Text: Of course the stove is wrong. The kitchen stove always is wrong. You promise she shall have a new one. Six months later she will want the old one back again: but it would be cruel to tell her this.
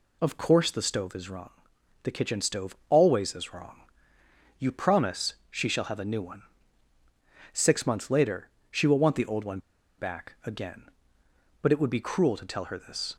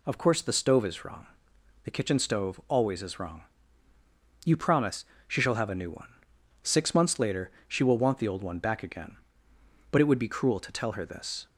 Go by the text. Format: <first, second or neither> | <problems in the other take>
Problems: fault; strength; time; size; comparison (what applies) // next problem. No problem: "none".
second | pauses between "promise" and "she"; slight; at 5.3 s; 0.16 s long; slight in the second // pauses between "later" and "she"; slight; at 8.4 s; 0.22 s long; slight in the second // pauses between "one" and "back"; at 9.5 s; 0.39 s long